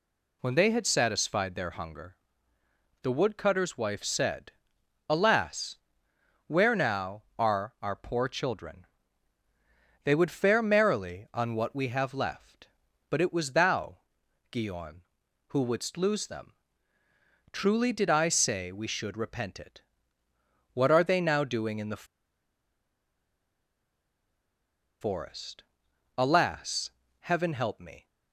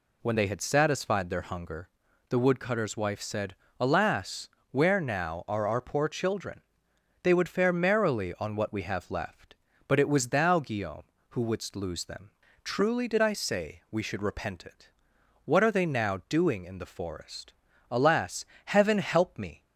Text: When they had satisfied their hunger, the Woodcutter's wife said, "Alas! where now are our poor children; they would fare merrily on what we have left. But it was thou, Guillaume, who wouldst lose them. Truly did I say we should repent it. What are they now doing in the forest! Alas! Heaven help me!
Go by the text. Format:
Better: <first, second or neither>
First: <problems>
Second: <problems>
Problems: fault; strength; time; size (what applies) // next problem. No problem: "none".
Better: second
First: pauses between "the" and "forest"; strong; at 22.0 s; 2.9 s long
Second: none